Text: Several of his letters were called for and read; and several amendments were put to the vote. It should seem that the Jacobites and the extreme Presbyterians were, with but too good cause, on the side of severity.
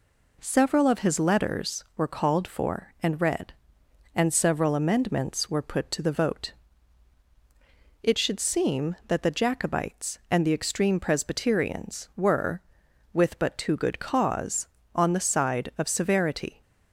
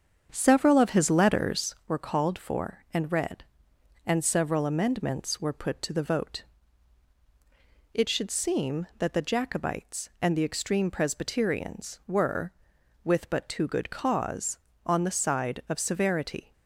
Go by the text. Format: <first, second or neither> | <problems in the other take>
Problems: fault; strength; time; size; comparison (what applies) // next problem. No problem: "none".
first | starts louder than the rest; strong; until 1.9 s; 7.5 dB